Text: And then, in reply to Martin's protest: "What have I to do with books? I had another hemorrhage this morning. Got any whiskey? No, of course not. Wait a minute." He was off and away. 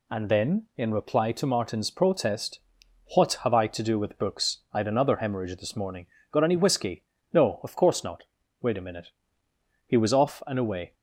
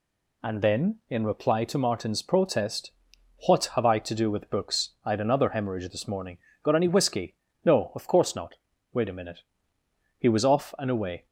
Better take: neither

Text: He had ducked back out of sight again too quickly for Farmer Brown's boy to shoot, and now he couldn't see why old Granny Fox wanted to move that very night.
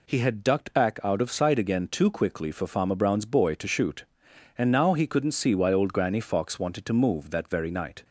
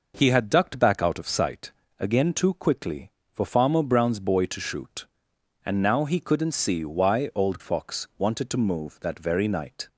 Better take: first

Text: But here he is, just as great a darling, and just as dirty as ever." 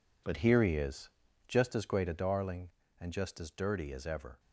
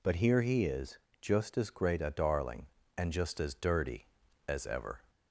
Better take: second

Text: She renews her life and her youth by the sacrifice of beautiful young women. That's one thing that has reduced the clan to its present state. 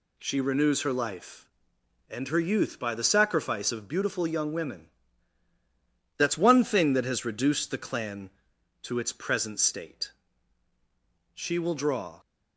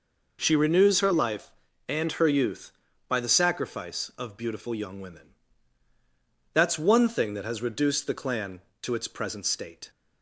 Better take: second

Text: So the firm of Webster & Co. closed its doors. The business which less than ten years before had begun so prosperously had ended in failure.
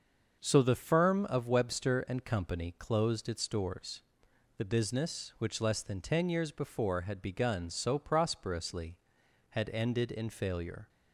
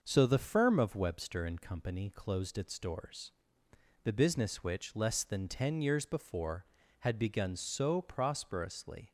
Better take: first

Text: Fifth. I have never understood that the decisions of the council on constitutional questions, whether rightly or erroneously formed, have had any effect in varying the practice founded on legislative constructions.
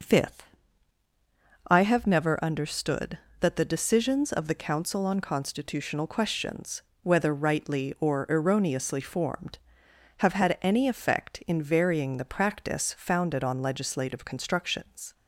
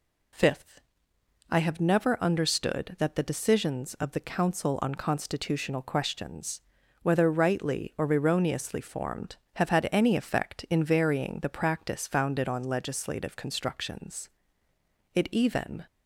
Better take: first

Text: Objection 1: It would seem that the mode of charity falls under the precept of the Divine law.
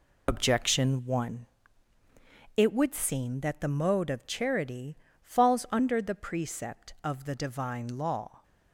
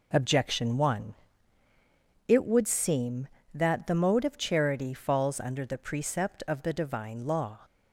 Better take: second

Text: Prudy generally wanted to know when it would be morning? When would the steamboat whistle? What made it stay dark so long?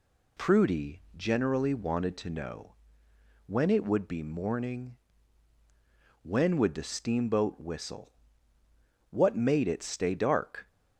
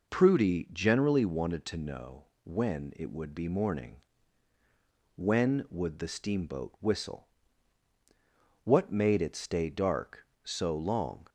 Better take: second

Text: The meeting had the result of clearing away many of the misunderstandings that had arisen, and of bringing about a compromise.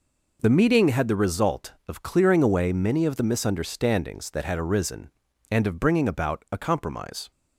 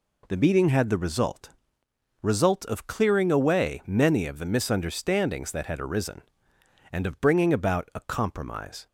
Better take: first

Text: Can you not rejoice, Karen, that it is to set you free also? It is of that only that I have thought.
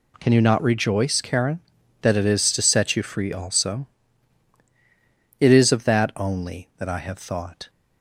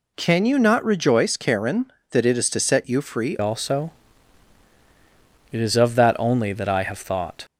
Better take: first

